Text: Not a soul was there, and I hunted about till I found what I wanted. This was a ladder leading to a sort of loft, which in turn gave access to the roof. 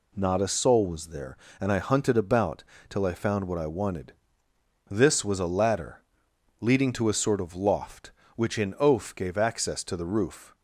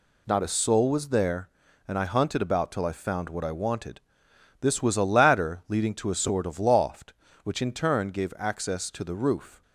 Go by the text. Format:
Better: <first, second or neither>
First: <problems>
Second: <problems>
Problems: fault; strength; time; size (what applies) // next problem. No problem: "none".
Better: second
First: pauses between "about" and "till"; slight; at 2.6 s; 0.26 s long // pauses between "ladder" and "leading"; noticeable; at 6.0 s; 0.60 s long // says "oaf" for "turn"; at 8.7 s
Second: none